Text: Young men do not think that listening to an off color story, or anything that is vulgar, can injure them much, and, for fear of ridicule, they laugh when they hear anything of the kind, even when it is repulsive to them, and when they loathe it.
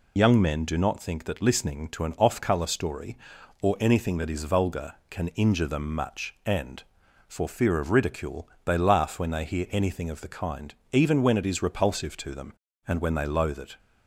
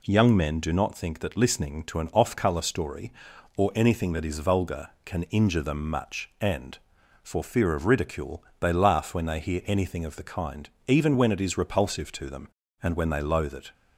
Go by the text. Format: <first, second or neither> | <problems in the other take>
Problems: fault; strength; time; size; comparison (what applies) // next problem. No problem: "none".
second | loses the start of "Young"; at 0.1 s; 75 ms